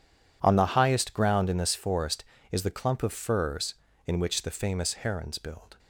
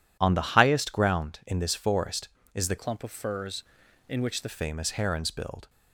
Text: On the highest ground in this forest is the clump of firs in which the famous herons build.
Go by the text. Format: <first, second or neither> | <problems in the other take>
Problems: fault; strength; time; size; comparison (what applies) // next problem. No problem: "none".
first | changes voice from "clump" to "the"; from 2.7 to 4.4 s; 1.7 s long